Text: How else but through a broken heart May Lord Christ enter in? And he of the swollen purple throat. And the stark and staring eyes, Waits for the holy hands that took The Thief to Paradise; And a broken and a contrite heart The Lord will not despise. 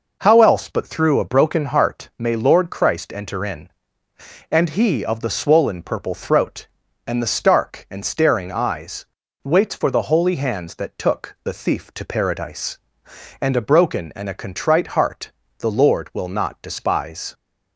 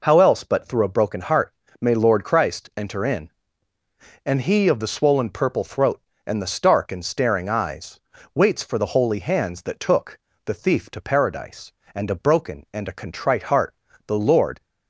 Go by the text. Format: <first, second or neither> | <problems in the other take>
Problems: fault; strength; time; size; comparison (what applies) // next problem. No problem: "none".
first | pauses between "heart" and "May"; slight; at 1.5 s; 0.26 s long // pauses between "took" and "The"; slight; at 10.1 s; 0.28 s long // pauses between "heart" and "The"; slight; at 13.7 s; 0.32 s long; slight in the first // stops before "will not despise"; at 14.6 s